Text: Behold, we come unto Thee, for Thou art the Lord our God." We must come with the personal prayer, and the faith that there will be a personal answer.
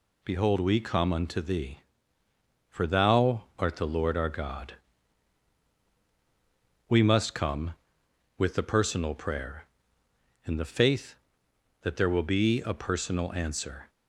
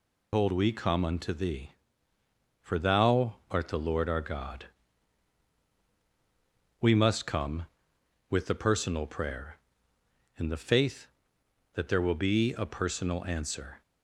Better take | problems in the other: first | loses the start of "Behold"; at 0.3 s; 170 ms

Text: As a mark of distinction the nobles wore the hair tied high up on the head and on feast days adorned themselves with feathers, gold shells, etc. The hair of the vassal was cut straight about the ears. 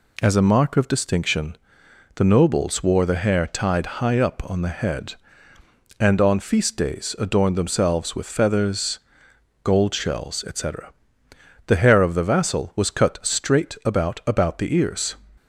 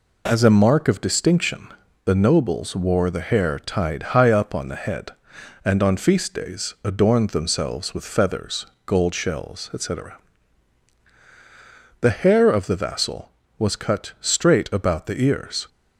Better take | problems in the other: second | pauses between "distinction" and "the"; noticeable; at 1.5 s; 0.58 s long; slight in the second // says "about" twice; at 14.2 s

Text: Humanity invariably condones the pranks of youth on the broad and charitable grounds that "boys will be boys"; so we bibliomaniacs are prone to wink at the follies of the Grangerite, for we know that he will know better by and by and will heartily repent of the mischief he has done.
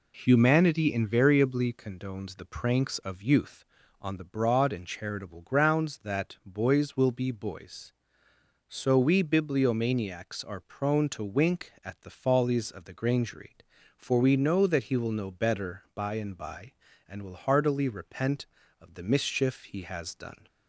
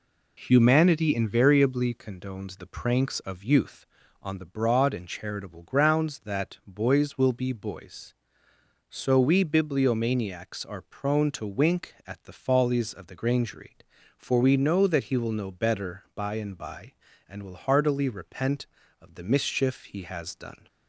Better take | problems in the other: neither | none

